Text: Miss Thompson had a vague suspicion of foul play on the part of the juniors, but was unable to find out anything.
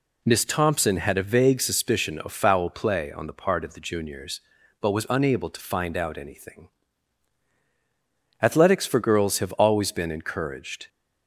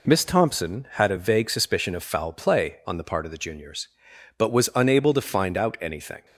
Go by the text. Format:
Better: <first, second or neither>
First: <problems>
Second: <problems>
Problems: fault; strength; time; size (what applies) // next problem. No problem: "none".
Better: second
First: goes on to say "Athletics for girls have always been encouraged"; strong; from 8.3 s on; 2.4 s long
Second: none